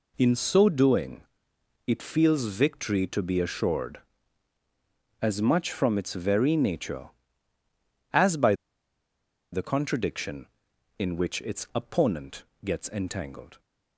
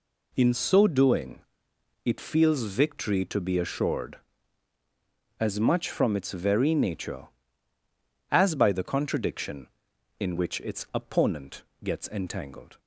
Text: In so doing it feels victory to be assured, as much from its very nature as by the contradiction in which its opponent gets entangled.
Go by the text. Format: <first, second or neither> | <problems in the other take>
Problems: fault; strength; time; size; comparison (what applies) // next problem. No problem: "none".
second | pauses between "doing" and "it"; noticeable; at 1.2 s; 0.66 s long; noticeable in the second // pauses between "by" and "the"; at 8.5 s; 0.98 s long // pauses between "opponent" and "gets"; slight; at 12.4 s; 0.18 s long; slight in the second